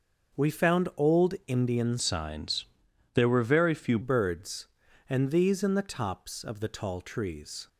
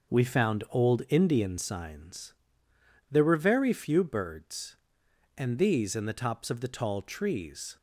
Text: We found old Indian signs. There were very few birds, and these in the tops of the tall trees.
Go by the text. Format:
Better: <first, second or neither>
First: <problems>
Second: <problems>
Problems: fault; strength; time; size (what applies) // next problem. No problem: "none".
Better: second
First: starts louder than the rest; noticeable; until 1.5 s; 6 dB // changes voice from "signs" to "few"; from 1.9 to 3.9 s; 2.0 s long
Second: starts louder than the rest; until 1.2 s; 6.5 dB